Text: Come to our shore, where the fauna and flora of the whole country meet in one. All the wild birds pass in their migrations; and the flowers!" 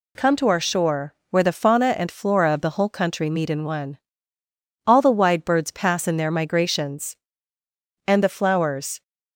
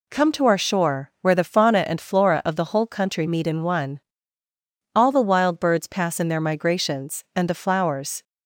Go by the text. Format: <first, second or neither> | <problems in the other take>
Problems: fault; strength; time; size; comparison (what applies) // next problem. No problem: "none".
second | says "wide" for "wild"; at 5.1 s